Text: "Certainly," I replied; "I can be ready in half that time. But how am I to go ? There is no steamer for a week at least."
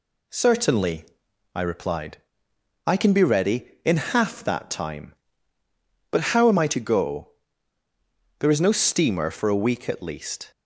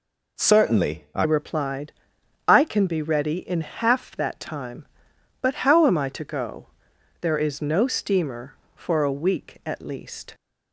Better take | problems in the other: first | changes voice at "replied"; from 1.2 s on; 9.1 s long

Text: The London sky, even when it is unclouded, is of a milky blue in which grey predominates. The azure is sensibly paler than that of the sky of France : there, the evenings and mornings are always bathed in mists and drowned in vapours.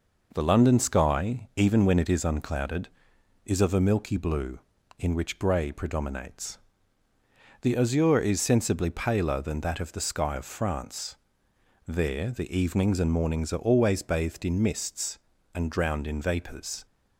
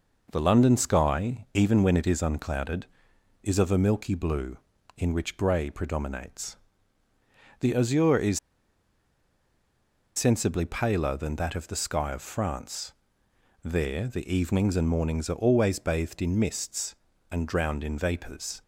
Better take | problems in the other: first | pauses between "is" and "sensibly"; strong; at 8.3 s; 1.7 s long

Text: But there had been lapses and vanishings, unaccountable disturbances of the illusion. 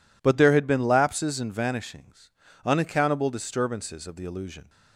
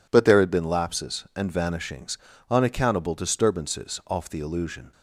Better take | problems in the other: first | says "off" for "of"; at 4.0 s

